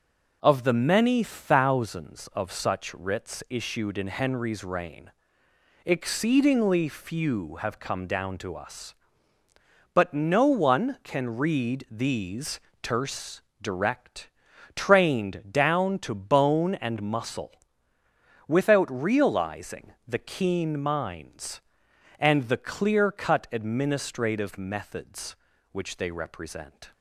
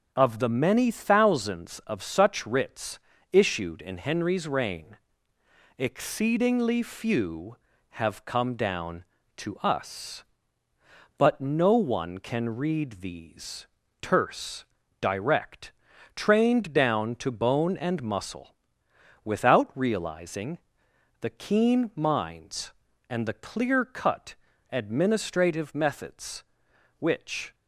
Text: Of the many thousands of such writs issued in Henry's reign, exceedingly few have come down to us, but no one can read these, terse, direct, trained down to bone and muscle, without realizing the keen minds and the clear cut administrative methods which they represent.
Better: first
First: pauses between "realizing" and "the"; slight; at 19.9 s; 0.16 s long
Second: starts louder than the rest; until 1.1 s; 6.5 dB // pauses between "writs" and "issued"; slight; at 2.9 s; 0.34 s long // pauses between "realizing" and "the"; noticeable; at 20.5 s; 0.62 s long // pauses between "cut" and "administrative"; slight; at 24.3 s; 0.36 s long // stops before "they represent"; at 27.5 s

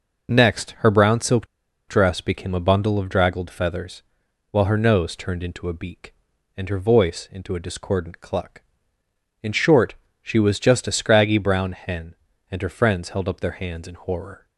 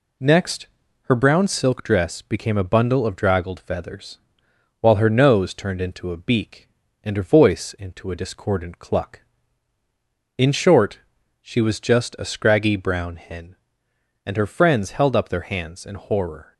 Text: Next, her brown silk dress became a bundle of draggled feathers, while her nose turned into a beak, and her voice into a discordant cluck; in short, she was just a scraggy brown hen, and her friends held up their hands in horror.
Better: second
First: pauses between "silk" and "dress"; at 1.4 s; 0.42 s long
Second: none

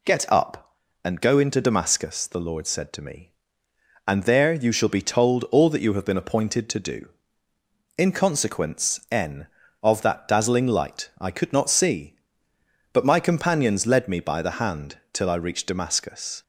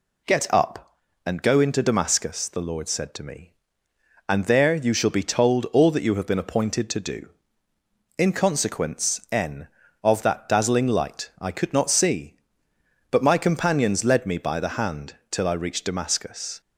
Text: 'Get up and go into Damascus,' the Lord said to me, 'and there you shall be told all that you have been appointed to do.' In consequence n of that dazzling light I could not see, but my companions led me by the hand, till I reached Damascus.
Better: neither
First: none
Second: none

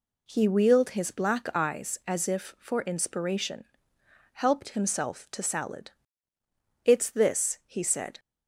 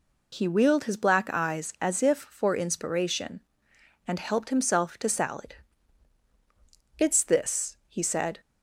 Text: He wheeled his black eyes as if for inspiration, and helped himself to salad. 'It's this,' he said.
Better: second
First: skips "and"; at 3.9 s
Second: none

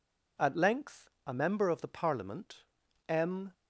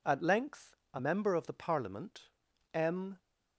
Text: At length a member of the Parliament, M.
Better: neither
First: pauses between "length" and "a"; slight; at 1.1 s; 0.16 s long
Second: pauses between "length" and "a"; slight; at 0.7 s; 0.18 s long

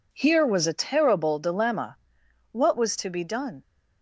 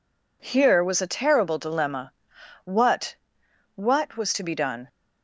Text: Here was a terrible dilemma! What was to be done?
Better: first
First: none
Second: says "What" twice; at 3.7 s

